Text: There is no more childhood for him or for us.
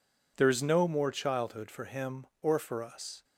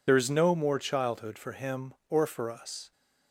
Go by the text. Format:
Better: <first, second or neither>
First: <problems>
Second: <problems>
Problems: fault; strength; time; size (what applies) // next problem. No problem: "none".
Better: first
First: none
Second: loses the start of "There"; at 0.0 s; 45 ms